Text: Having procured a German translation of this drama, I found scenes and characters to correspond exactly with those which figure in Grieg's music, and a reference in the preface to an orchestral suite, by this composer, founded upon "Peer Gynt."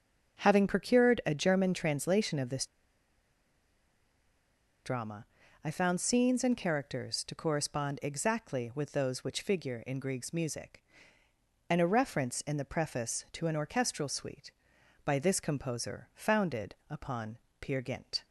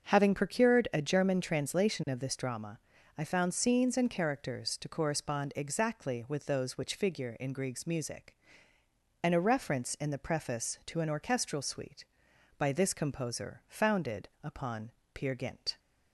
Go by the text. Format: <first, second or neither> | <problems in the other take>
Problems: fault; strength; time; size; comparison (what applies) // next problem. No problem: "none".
second | starts louder than the rest; until 1.4 s; 6.5 dB; also in the second // pauses between "this" and "drama"; strong; at 2.6 s; 2.1 s long // pauses between "upon" and "Peer"; slight; at 17.3 s; 0.20 s long; slight in the second